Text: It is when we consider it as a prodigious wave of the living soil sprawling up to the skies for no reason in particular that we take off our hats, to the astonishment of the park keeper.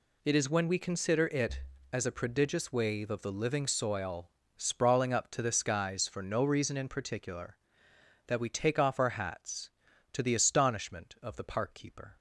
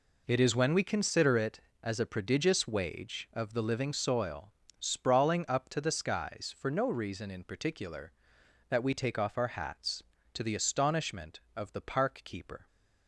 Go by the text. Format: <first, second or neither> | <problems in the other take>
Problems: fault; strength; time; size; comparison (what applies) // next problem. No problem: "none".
first | says "wage" for "wave"; at 2.6 s // pauses between "soil" and "sprawling"; slight; at 4.5 s; 0.26 s long; slight in the first